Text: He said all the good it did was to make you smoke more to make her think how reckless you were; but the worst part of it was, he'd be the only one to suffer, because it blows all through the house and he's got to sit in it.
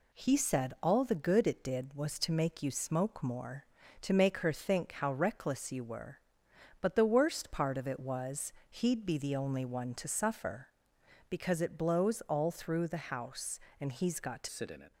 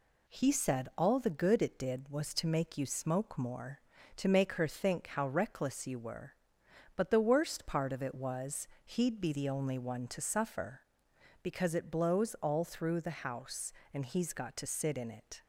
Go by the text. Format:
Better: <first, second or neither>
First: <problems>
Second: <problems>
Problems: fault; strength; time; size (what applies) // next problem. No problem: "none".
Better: second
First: changes voice at "sit"; from 14.4 s on; 0.5 s long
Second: none